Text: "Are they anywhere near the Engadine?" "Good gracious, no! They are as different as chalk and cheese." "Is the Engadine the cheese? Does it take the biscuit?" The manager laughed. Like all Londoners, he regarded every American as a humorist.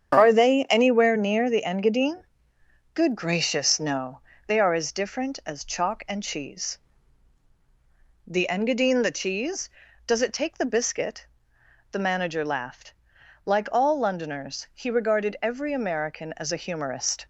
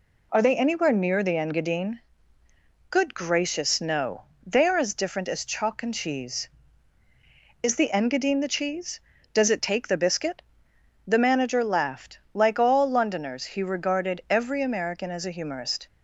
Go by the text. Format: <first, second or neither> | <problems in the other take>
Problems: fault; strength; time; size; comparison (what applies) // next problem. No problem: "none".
second | starts louder than the rest; strong; until 1.1 s; 8 dB // skips "Is"; at 7.5 s